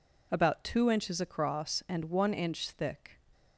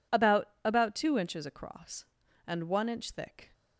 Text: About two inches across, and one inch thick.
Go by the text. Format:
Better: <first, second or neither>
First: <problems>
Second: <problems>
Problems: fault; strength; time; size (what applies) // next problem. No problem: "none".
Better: first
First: none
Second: says "About" twice; at 0.6 s